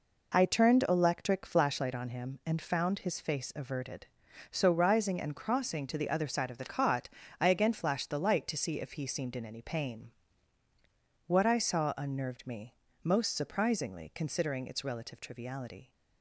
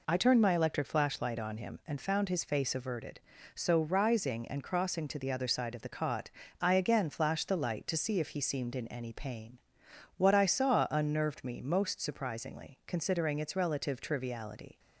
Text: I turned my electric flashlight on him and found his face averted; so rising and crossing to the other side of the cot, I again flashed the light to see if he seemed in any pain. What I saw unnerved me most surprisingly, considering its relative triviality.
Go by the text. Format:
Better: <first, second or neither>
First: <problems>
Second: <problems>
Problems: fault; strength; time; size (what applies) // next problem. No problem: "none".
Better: second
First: skips "my"; at 0.8 s // pauses between "me" and "most"; slight; at 12.7 s; 0.30 s long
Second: none